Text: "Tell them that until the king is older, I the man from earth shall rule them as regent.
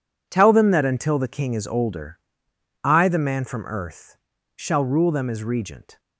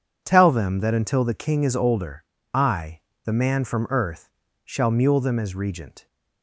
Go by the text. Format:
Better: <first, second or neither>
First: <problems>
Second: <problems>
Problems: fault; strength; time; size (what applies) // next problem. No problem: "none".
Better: first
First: pauses between "earth" and "shall"; at 4.1 s; 0.40 s long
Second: pauses between "I" and "the"; slight; at 3.0 s; 0.24 s long // pauses between "earth" and "shall"; slight; at 4.2 s; 0.34 s long // says "mule" for "rule"; at 4.9 s